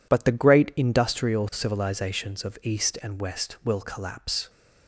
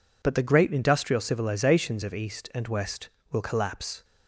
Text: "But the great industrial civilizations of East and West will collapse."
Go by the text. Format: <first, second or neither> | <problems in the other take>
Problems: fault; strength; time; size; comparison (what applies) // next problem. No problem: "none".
neither | none